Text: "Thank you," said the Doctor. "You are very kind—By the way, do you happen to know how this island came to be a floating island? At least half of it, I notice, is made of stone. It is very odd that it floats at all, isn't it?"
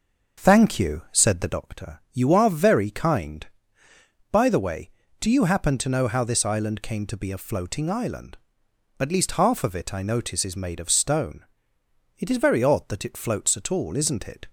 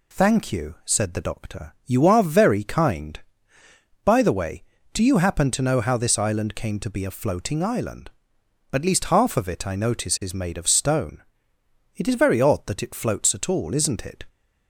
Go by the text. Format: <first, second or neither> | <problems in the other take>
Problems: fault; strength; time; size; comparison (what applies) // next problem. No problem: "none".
second | starts louder than the rest; until 1.6 s; 6 dB